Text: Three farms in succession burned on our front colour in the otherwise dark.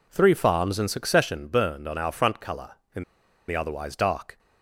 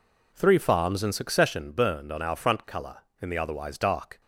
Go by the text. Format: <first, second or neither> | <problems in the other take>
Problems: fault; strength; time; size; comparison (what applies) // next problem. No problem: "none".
second | pauses between "in" and "the"; noticeable; at 3.0 s; 0.46 s long